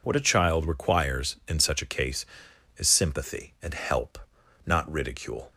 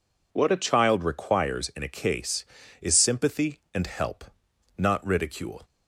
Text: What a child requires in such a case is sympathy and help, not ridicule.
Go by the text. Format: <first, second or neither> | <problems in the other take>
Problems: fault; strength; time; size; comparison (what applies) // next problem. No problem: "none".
first | skips "such"; at 1.8 s